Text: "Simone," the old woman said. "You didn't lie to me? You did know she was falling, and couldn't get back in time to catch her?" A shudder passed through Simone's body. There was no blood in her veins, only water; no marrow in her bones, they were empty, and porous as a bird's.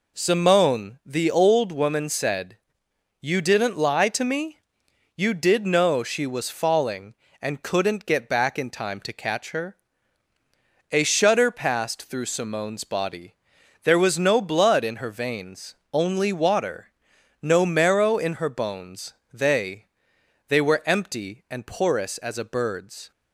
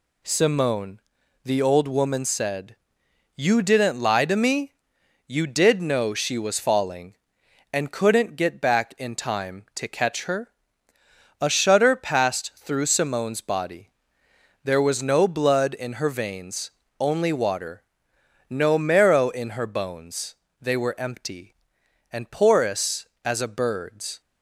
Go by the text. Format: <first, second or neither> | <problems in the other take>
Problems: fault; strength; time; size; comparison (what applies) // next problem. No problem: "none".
second | says "they" twice; at 20.4 s